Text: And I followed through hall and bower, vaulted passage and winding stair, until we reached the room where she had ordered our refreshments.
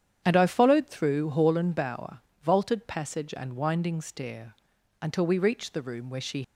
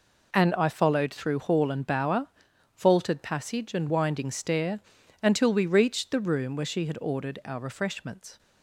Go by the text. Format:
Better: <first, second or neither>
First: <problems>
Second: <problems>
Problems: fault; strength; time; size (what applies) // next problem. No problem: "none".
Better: second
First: starts louder than the rest; strong; until 1.2 s; 9 dB // stops before "had ordered our refreshments"; at 6.4 s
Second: none